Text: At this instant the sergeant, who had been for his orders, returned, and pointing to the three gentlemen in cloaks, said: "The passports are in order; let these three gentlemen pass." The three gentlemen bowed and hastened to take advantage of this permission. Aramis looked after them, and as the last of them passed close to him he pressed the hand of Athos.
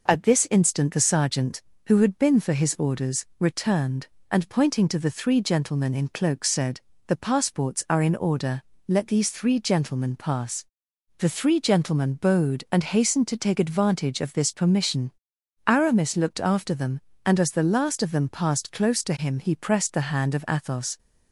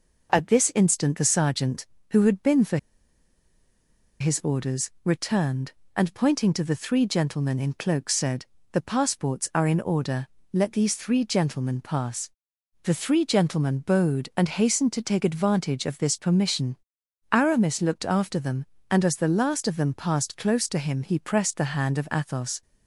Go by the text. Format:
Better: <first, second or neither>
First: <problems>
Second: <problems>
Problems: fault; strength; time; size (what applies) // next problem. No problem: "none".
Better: first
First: none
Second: pauses between "for" and "his"; strong; at 2.7 s; 1.4 s long